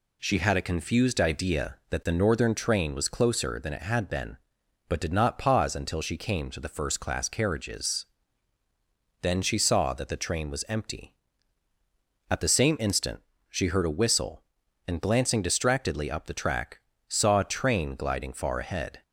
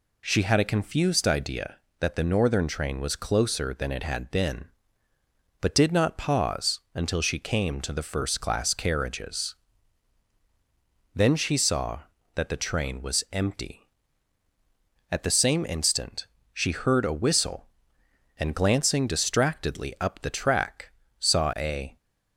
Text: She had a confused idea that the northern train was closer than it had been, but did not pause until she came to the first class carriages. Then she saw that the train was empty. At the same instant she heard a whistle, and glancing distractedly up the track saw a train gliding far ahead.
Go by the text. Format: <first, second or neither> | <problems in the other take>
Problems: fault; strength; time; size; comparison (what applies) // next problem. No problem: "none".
first | pauses between "instant" and "she"; slight; at 16.2 s; 0.28 s long; slight in the first // pauses between "track" and "saw"; slight; at 20.8 s; 0.32 s long; slight in the first // stops before "train gliding far ahead"; at 21.9 s